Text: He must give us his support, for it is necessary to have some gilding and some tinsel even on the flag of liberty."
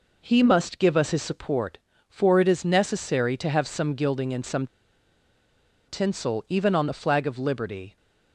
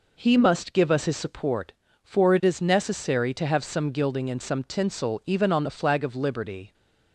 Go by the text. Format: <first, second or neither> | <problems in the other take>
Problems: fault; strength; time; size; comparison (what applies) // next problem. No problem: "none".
second | pauses between "some" and "tinsel"; at 4.6 s; 1.2 s long